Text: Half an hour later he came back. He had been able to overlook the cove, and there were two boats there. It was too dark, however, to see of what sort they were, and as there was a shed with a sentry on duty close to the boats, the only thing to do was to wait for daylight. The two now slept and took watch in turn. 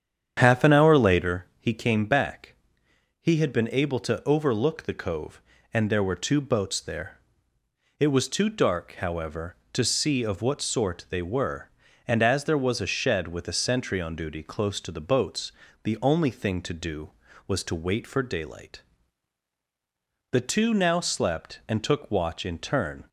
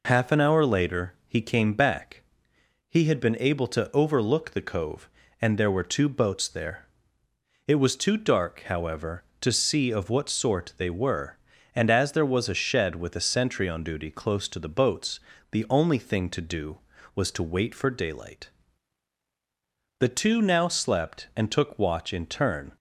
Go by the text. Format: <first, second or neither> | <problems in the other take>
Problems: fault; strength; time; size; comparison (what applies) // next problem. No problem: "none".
second | starts louder than the rest; strong; until 1.5 s; 8.5 dB